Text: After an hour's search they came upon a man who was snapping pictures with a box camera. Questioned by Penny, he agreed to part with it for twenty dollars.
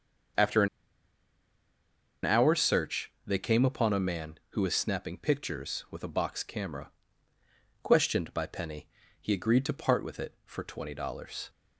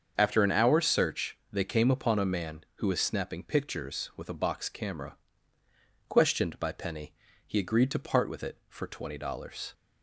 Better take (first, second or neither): second